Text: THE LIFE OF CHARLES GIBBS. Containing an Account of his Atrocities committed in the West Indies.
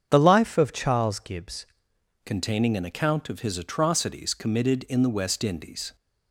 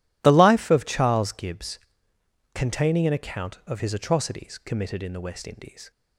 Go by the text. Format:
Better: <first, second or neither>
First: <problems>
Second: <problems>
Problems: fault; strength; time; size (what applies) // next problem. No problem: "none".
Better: second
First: starts louder than the rest; strong; until 1.1 s; 7.5 dB // changes voice at "Containing"; from 2.2 s on; 3.7 s long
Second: none